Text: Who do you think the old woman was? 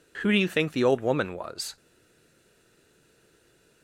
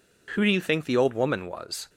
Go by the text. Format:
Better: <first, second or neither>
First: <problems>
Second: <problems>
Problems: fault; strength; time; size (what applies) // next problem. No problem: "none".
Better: second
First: stays silent after the last word; noticeable; from 1.7 s on; 2.1 s long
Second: none